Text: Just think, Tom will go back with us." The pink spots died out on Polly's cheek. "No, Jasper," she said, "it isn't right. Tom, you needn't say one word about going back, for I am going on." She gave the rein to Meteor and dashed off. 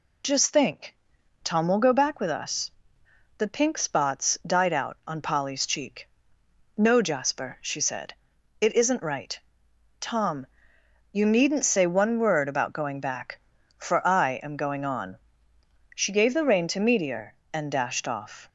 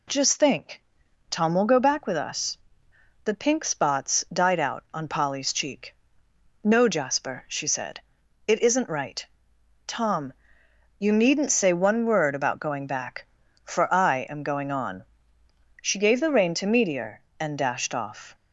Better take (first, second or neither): second